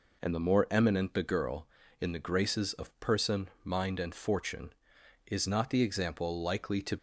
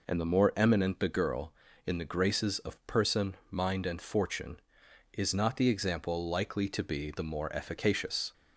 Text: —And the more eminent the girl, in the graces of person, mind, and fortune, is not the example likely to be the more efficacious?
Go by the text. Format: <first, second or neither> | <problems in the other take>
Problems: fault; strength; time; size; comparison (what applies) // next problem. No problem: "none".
second | stops before "be the more efficacious"; at 6.9 s